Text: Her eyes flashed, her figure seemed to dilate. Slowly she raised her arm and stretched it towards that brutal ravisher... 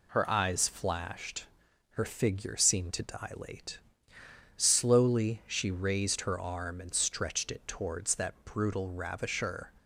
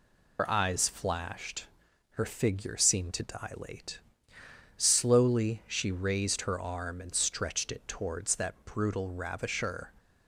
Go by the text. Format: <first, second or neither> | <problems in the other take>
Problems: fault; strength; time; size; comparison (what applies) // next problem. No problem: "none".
first | loses the start of "Her"; at 0.3 s; 80 ms